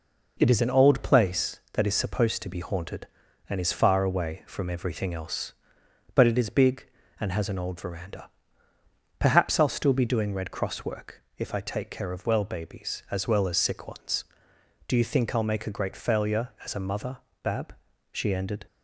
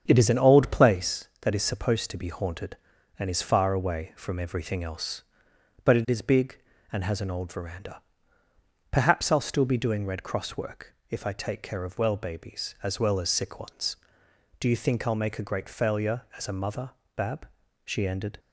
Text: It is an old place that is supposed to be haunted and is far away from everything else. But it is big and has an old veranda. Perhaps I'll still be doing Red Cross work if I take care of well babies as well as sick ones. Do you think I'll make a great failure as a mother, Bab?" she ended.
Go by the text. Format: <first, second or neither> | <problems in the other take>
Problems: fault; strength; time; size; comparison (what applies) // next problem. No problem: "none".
first | starts louder than the rest; strong; until 1.0 s; 7.5 dB // pauses between "work" and "if"; slight; at 10.9 s; 0.16 s long; slight in the first